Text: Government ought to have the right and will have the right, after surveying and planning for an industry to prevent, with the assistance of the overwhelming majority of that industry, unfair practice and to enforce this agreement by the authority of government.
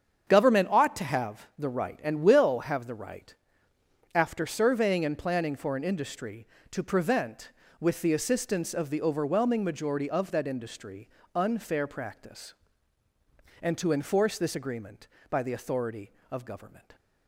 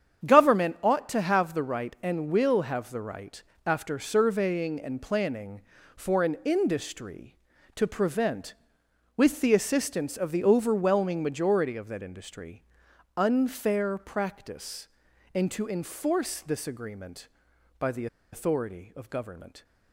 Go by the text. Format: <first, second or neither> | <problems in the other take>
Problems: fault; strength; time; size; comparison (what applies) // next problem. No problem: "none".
first | starts louder than the rest; strong; until 1.3 s; 8 dB; strong in the first // pauses between "the" and "authority"; slight; at 18.0 s; 0.26 s long